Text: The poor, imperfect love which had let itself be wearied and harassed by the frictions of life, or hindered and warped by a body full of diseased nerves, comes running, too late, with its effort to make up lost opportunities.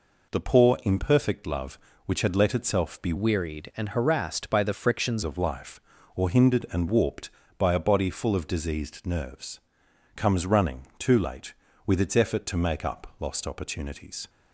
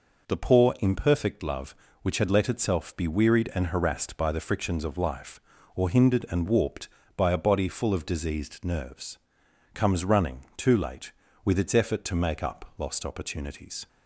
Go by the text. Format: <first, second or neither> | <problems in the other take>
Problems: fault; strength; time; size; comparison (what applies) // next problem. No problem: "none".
second | changes voice from "wearied" to "frictions"; from 3.1 to 5.2 s; 2.1 s long